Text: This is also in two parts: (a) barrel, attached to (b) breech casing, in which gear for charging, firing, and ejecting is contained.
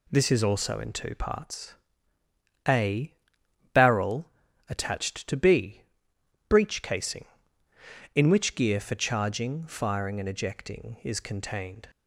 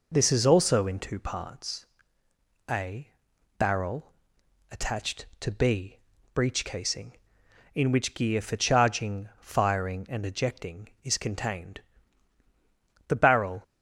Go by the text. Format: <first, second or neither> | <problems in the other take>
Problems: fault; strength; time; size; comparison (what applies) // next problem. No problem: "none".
first | goes on to say "The barrel"; from 13.0 s on; 0.56 s long